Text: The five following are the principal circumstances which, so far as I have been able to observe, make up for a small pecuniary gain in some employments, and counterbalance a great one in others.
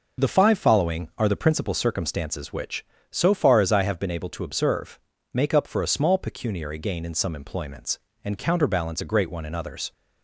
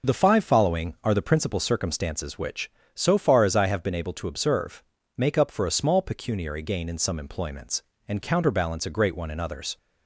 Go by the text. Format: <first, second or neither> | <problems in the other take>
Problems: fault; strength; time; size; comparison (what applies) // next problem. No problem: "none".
neither | none